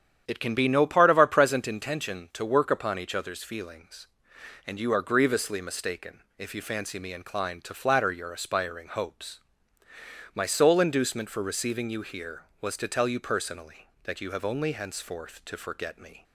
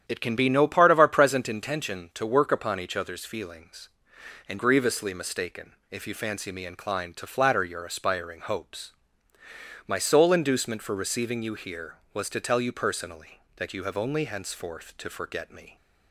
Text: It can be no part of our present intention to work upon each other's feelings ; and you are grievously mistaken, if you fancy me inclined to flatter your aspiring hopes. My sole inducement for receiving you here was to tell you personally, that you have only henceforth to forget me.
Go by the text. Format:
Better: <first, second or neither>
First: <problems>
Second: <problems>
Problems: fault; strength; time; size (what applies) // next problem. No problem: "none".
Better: first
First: starts louder than the rest; strong; until 1.3 s; 9 dB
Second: starts louder than the rest; strong; until 1.1 s; 9.5 dB // skips "you are"; at 4.5 s